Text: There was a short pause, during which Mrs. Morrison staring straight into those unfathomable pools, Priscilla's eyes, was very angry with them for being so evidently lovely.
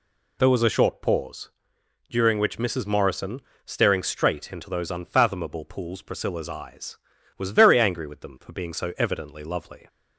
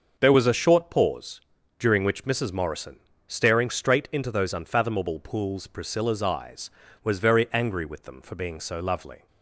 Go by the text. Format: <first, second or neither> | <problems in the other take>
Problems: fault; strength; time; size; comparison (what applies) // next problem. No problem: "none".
first | starts louder than the rest; until 1.2 s; 6.5 dB // pauses between "Morrison" and "staring"; slight; at 3.0 s; 0.26 s long; slight in the first // skips "evidently"; at 8.7 s